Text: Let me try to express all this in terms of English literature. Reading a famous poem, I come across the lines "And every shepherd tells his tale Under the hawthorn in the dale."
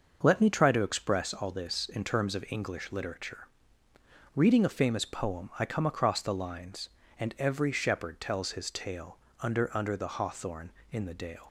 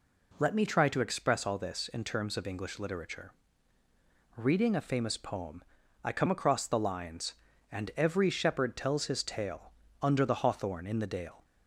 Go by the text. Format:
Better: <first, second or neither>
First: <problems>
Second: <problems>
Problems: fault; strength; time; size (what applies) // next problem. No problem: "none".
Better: second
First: starts louder than the rest; noticeable; until 1.2 s; 6 dB // pauses between "tale" and "Under"; slight; at 9.1 s; 0.24 s long // says "Under" twice; at 9.7 s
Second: pauses between "tale" and "Under"; slight; at 9.7 s; 0.28 s long